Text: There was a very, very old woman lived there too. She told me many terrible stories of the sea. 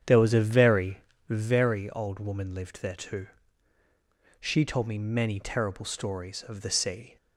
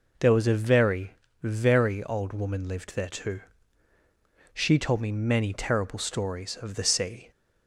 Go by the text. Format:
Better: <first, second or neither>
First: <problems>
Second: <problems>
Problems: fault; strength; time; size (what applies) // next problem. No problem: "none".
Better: second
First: starts louder than the rest; strong; until 1.6 s; 8.5 dB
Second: none